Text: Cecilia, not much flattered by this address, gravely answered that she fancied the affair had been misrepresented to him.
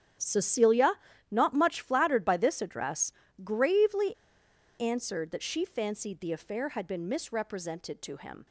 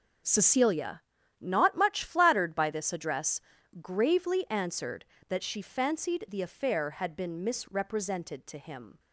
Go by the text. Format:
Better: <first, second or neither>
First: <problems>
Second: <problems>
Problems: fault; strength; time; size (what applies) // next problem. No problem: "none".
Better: second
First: starts louder than the rest; strong; until 1.5 s; 10 dB // pauses between "gravely" and "answered"; noticeable; at 4.1 s; 0.64 s long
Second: starts louder than the rest; until 1.6 s; 7 dB